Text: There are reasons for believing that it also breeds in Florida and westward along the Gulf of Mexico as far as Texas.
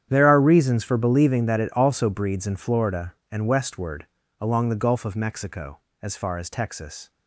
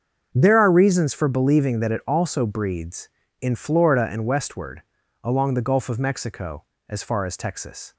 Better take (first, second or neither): second